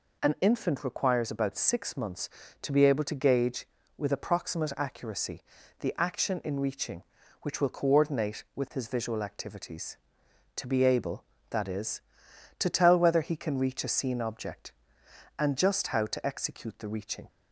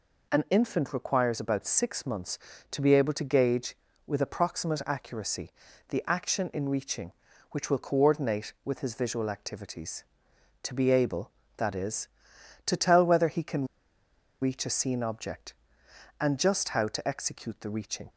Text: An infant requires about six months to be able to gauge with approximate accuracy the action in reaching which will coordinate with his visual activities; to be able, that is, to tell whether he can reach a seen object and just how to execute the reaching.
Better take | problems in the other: first | pauses between "accuracy" and "the"; at 5.5 s; 0.38 s long; also in the first // pauses between "can" and "reach"; noticeable; at 13.6 s; 0.77 s long

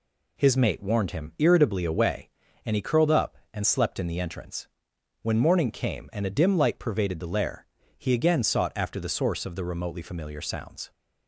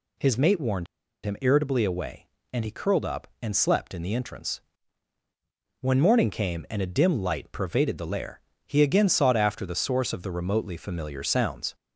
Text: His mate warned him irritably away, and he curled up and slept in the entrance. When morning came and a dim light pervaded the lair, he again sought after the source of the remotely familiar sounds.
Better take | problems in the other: first | pauses between "warned" and "him"; at 0.8 s; 0.38 s long

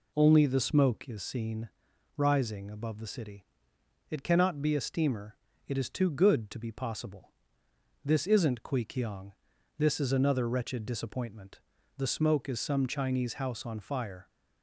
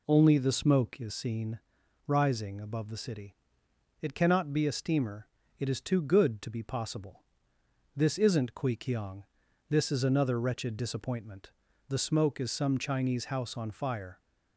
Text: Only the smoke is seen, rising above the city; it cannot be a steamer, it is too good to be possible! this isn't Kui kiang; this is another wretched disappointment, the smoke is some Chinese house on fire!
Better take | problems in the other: neither | none

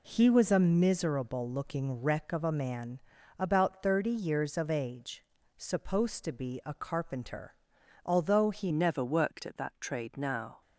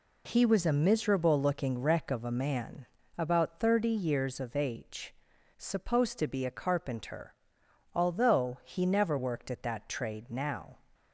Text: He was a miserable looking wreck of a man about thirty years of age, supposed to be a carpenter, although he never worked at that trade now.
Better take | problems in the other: second | pauses between "man" and "about"; at 2.9 s; 0.40 s long; slight in the second // changes voice at "never"; from 8.7 s on; 1.9 s long

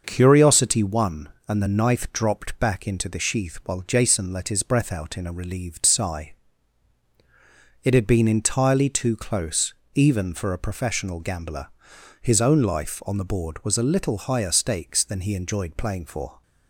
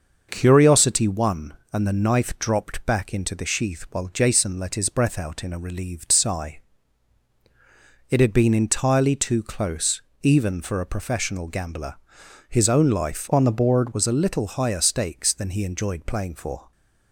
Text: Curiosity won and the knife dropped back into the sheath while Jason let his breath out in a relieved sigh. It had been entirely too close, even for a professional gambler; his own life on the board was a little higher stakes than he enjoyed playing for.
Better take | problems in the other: first | starts louder than the rest; noticeable; until 1.3 s; 6 dB; noticeable in the first // changes voice from "on" to "board"; from 13.3 to 13.9 s; 0.6 s long

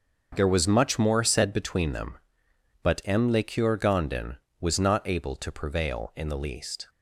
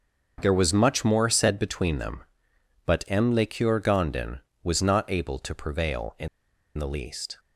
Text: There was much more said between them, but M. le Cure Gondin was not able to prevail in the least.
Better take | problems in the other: first | starts louder than the rest; until 1.4 s; 6.5 dB; also in the first // pauses between "in" and "the"; noticeable; at 6.2 s; 0.50 s long

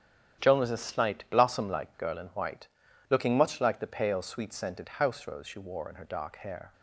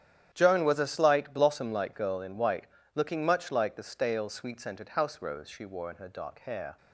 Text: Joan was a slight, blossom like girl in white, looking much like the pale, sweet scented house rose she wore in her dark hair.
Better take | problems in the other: first | starts louder than the rest; strong; until 1.3 s; 11 dB; strong in the first // says "stale" for "pale"; at 3.8 s

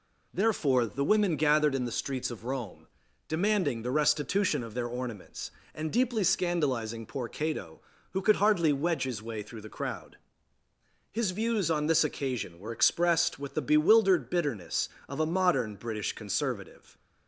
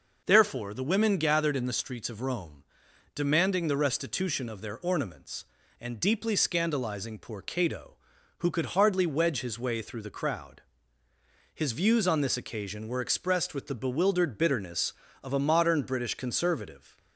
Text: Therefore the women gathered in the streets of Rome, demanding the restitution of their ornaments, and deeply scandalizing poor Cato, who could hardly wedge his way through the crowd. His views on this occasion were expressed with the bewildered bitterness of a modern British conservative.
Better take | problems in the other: neither | none

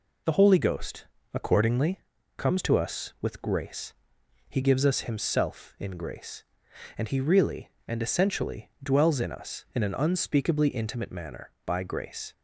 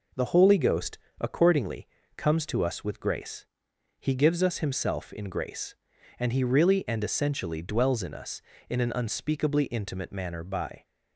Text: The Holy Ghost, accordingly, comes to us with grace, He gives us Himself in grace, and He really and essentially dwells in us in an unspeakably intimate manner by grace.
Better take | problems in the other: first | stops before "grace"; at 10.8 s

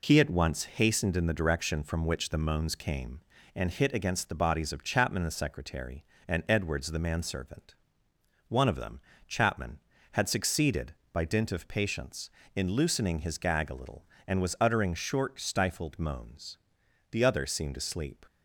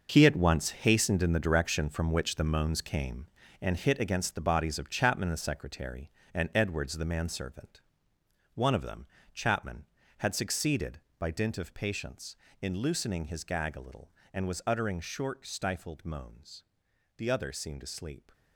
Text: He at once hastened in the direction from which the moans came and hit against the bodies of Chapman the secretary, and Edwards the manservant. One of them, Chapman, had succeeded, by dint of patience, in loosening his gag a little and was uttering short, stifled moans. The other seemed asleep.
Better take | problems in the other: first | gets quieter; strong; throughout; 11 dB

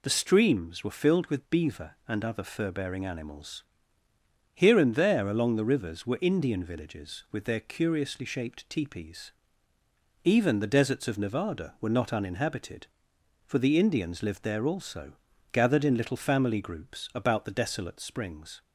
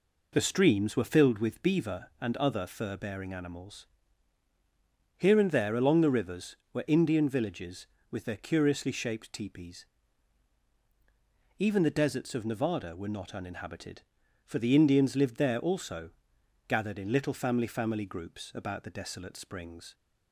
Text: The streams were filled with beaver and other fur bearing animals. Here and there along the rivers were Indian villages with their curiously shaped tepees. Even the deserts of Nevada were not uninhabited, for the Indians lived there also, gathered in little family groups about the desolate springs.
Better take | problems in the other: first | says "family" twice; at 17.6 s

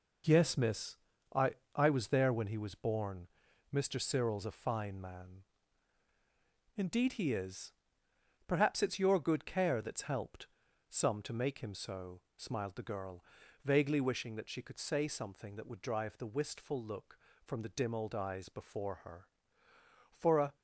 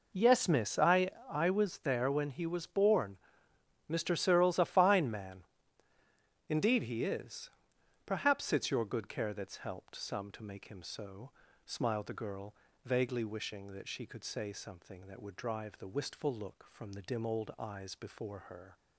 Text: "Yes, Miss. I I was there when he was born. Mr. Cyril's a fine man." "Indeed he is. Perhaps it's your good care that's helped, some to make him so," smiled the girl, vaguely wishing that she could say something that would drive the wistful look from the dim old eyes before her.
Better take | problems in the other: second | pauses between "I" and "I"; slight; at 1.5 s; 0.22 s long; slight in the second // goes on to say "For a"; slight; from 20.1 s on; 0.44 s long

